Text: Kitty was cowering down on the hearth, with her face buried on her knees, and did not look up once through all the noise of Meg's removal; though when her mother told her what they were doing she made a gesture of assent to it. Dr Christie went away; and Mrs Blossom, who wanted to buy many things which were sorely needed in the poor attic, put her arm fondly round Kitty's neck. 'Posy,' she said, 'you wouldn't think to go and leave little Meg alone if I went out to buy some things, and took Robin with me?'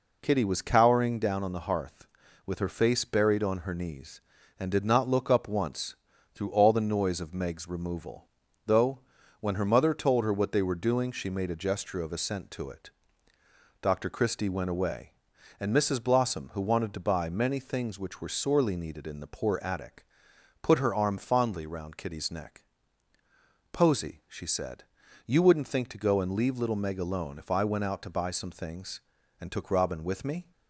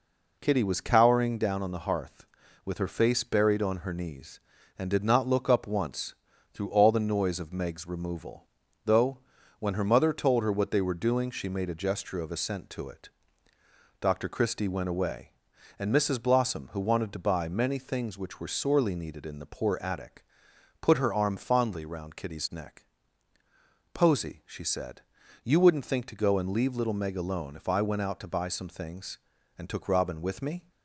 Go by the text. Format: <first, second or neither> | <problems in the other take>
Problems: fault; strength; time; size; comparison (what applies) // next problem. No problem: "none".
neither | pauses between "once" and "through"; the same in both // pauses between "though" and "when"; the same in both